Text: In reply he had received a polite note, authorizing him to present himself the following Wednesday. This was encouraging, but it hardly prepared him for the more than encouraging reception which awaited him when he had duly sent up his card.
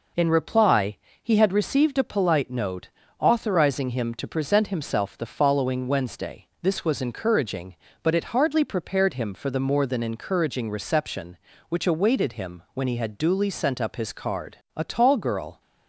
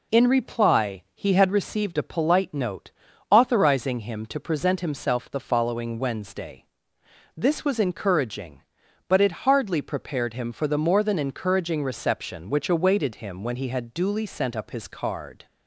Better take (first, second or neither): second